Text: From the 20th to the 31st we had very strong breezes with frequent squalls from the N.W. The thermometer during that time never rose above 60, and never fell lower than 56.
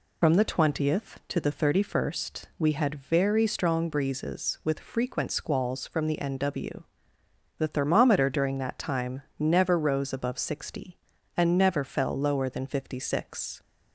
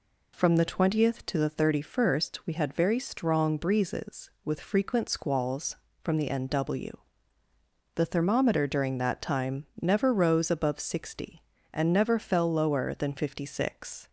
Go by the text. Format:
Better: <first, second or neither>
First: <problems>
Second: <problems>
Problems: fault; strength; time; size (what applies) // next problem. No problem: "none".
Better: second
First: loses the start of "From"; at 0.2 s; 65 ms // pauses between "time" and "never"; slight; at 9.2 s; 0.18 s long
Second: none